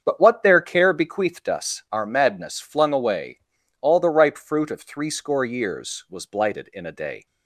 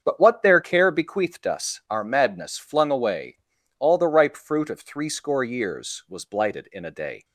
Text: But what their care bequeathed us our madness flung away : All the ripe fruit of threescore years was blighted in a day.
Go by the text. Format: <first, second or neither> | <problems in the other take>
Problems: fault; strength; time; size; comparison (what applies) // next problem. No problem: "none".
neither | starts louder than the rest; strong; the same in both